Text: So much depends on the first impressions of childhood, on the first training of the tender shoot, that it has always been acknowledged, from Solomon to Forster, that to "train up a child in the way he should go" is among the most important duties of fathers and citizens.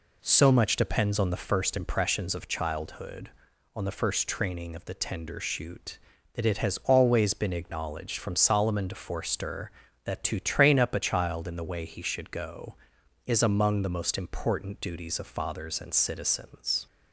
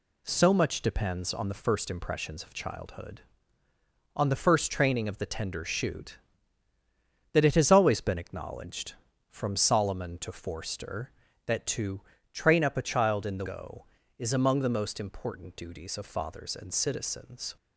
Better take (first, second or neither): first